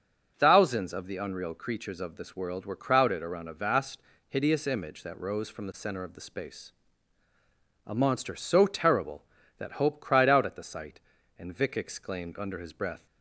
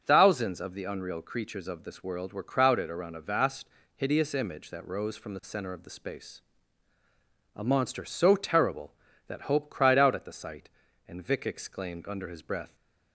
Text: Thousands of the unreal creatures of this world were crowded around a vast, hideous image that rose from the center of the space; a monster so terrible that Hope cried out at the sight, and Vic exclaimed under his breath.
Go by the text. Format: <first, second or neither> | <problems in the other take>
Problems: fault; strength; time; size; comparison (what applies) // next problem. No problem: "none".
neither | starts louder than the rest; the same in both